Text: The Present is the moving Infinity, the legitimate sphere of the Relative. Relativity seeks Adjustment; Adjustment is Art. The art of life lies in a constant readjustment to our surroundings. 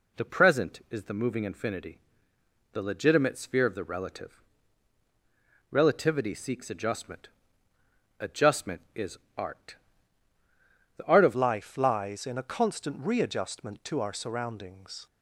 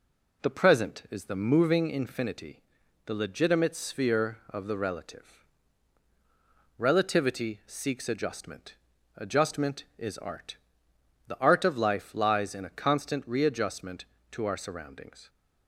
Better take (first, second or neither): second